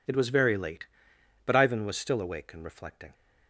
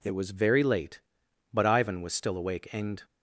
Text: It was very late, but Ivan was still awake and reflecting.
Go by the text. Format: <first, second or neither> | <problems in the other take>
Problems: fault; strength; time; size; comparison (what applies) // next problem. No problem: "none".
first | stops before "reflecting"; at 3.0 s